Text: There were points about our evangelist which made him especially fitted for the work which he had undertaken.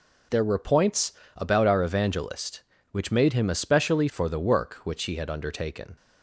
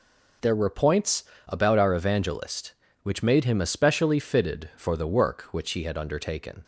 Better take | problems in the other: second | pauses between "points" and "about"; slight; at 1.1 s; 0.24 s long; slight in the second // skips "fitted"; at 4.0 s

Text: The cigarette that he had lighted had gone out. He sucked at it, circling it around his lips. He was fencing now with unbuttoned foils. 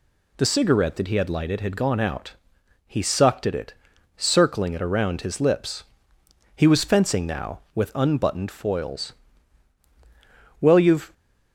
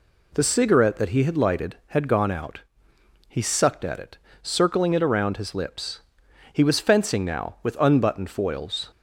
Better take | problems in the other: second | goes on to say "Well you've"; from 10.6 s on; 0.52 s long

